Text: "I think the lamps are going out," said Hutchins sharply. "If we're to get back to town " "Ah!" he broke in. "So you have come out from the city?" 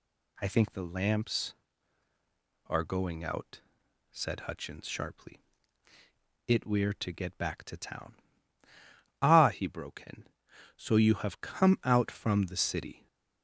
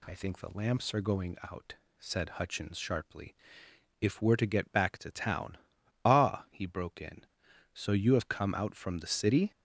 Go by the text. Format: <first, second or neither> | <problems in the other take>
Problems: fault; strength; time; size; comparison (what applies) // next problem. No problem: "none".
second | says "It" for "If"; at 6.4 s